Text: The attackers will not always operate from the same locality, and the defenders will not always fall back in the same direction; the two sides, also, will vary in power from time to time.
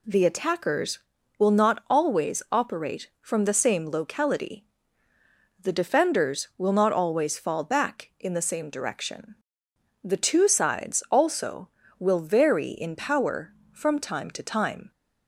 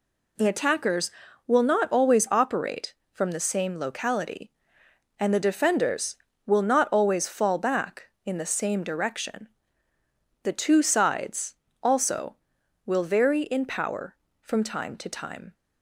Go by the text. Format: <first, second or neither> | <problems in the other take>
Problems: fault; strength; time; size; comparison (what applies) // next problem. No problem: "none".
second | skips "and"; at 5.1 s